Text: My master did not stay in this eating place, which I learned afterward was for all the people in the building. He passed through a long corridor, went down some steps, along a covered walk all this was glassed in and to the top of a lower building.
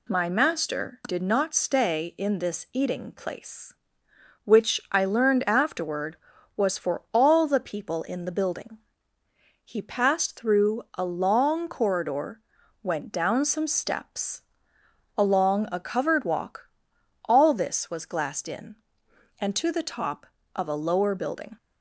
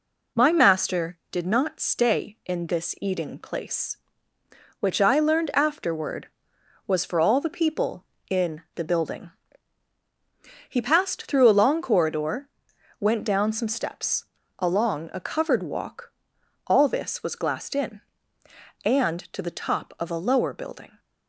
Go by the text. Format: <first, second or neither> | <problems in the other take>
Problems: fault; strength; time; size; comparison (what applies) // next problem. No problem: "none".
neither | pauses between "walk" and "all"; noticeable; the same in both